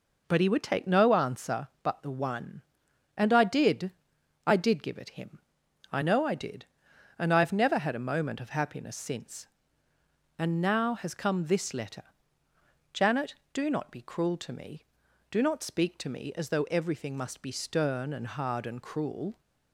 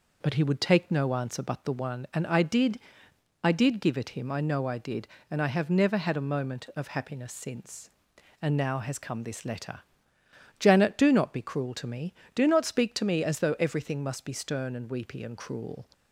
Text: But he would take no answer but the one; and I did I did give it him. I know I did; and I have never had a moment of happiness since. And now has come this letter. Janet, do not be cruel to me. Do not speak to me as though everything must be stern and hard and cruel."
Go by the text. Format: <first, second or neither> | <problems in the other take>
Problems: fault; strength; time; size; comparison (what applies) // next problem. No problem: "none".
first | pauses between "did" and "I"; noticeable; at 2.7 s; 0.64 s long; noticeable in the first // says "weepy" for "hard"; at 14.9 s